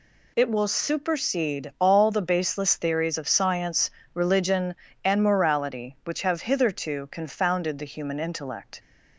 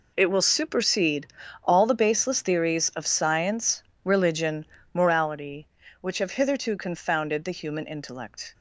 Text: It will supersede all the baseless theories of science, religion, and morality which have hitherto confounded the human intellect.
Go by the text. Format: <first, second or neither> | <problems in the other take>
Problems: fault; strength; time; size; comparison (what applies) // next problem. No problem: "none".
first | pauses between "supersede" and "all"; at 1.2 s; 0.38 s long // skips "and"; at 4.7 s